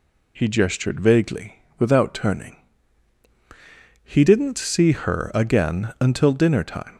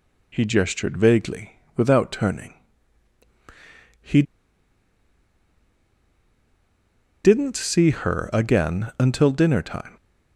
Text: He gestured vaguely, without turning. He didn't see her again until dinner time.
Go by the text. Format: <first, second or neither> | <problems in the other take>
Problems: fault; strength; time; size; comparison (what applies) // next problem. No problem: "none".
first | pauses between "He" and "didn't"; strong; at 4.2 s; 3.0 s long